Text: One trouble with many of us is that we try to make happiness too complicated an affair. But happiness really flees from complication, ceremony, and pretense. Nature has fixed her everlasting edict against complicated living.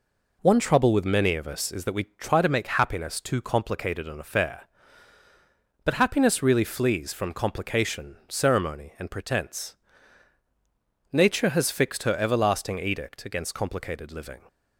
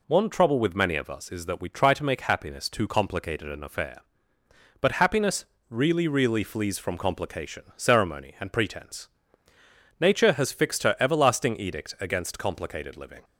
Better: first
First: none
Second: pauses between "happiness" and "really"; slight; at 5.4 s; 0.24 s long // says "really" twice; at 6.0 s

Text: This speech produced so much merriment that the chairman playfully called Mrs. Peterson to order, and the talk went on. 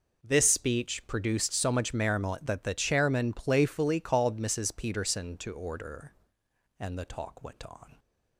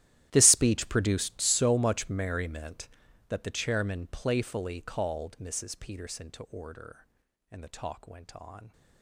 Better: first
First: none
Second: gets quieter; strong; throughout; 20 dB

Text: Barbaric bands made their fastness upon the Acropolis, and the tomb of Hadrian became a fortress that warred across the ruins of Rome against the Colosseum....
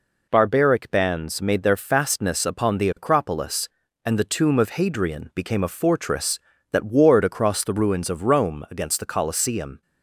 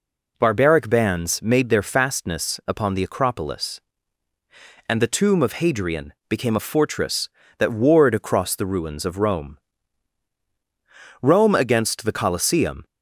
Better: first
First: none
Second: pauses between "Hadrian" and "became"; slight; at 6.1 s; 0.16 s long // says "Rome" twice; at 11.2 s

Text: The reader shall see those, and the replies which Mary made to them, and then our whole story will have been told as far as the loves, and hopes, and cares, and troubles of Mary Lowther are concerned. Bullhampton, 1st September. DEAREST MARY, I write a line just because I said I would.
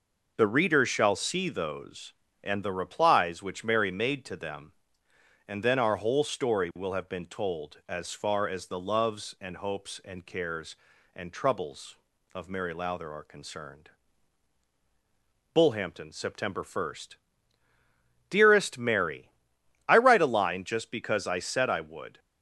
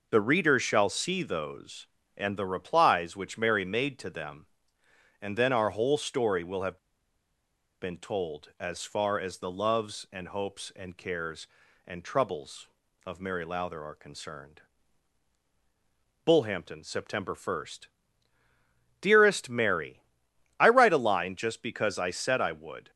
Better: first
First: none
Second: pauses between "have" and "been"; at 6.7 s; 1.0 s long

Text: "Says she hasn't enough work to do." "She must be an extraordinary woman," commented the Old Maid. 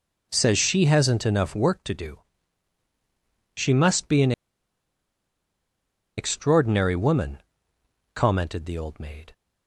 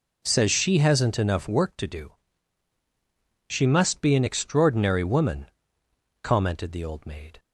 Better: second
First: pauses between "an" and "extraordinary"; strong; at 4.3 s; 1.8 s long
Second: none

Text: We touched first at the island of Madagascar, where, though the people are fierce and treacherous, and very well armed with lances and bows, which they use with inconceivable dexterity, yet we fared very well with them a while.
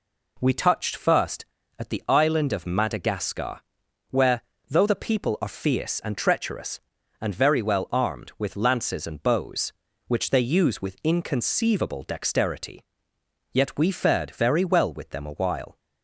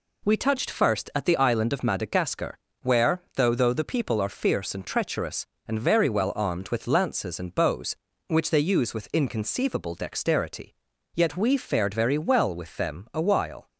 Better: first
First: none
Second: says "though" twice; at 3.5 s

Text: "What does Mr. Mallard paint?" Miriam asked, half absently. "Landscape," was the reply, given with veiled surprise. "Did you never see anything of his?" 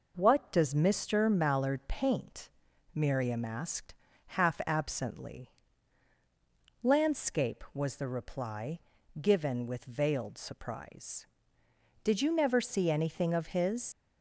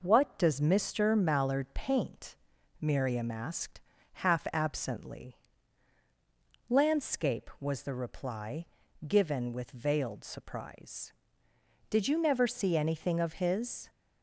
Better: second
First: leaves "his" unfinished; at 13.9 s; 115 ms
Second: none

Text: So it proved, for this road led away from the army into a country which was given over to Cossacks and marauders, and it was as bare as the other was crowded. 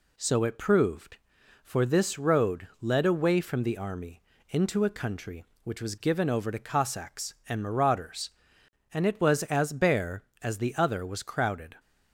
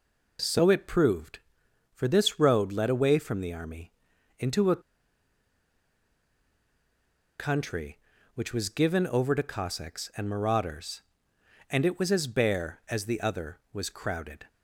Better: first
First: pauses between "army" and "into"; slight; at 4.2 s; 0.28 s long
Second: pauses between "army" and "into"; noticeable; at 3.9 s; 0.46 s long // pauses between "a" and "country"; strong; at 4.8 s; 2.5 s long

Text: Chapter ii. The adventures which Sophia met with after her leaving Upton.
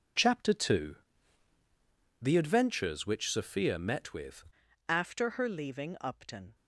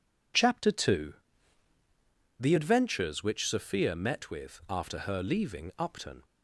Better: second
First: changes voice at "after"; from 4.8 s on; 1.7 s long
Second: none

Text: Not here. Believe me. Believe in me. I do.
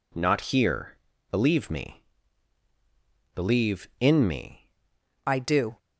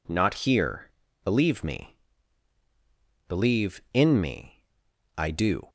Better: second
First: changes voice at "I"; from 5.2 s on; 0.5 s long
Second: none

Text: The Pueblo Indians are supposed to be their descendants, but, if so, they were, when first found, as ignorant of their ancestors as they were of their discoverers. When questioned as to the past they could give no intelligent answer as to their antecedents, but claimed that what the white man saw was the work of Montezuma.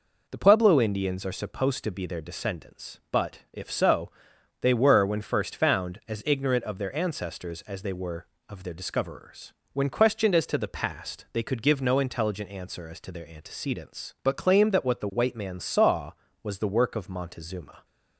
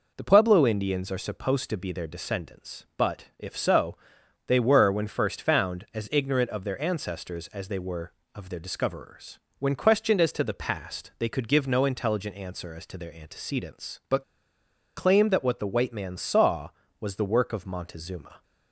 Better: first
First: none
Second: pauses between "but" and "claimed"; noticeable; at 14.2 s; 0.75 s long

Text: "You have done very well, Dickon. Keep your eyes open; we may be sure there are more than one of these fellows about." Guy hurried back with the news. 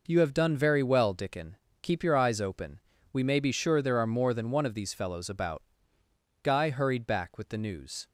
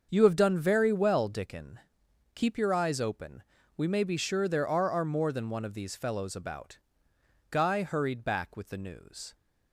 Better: first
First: none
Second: starts louder than the rest; until 1.1 s; 6.5 dB // says "are" twice; at 4.9 s

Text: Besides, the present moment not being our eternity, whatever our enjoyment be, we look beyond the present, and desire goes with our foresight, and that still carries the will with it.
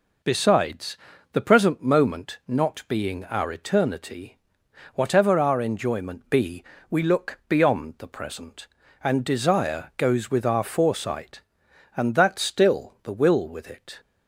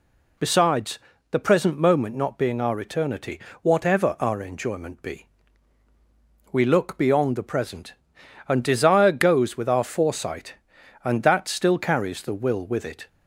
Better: second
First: skips "carries"; at 12.9 s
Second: none

